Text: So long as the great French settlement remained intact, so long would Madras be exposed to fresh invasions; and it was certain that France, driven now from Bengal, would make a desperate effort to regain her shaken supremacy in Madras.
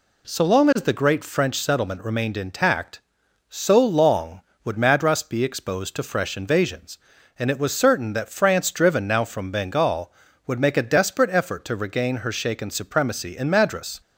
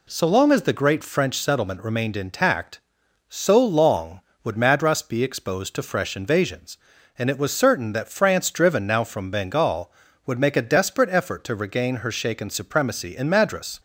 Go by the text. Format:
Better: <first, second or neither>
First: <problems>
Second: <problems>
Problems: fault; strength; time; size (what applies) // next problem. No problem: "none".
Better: neither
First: none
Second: none